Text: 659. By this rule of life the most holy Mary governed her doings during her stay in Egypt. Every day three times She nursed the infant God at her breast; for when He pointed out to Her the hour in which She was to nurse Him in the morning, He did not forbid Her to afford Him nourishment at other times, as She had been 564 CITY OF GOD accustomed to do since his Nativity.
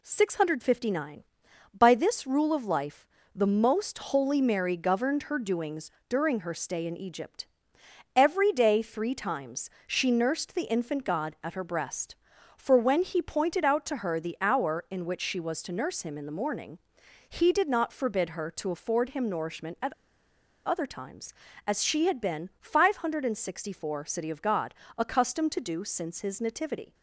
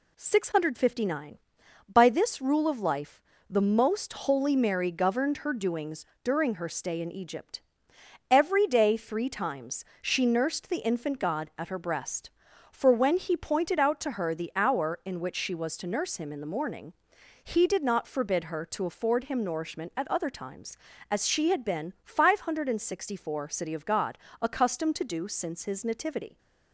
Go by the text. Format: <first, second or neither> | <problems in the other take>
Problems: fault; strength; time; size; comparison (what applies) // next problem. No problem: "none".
second | pauses between "life" and "the"; slight; at 3.0 s; 0.28 s long; slight in the second // pauses between "doings" and "during"; slight; at 5.9 s; 0.18 s long; slight in the second // pauses between "times" and "She"; slight; at 9.6 s; 0.18 s long; slight in the second // pauses between "at" and "other"; noticeable; at 19.9 s; 0.75 s long // pauses between "GOD" and "accustomed"; slight; at 24.7 s; 0.24 s long; slight in the second